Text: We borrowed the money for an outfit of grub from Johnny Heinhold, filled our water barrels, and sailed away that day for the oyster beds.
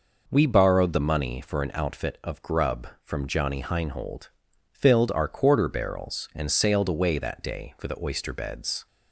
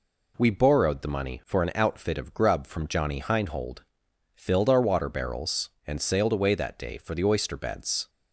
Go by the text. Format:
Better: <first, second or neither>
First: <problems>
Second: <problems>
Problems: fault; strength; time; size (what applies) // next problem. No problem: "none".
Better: second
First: says "quarter" for "water"; at 5.2 s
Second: none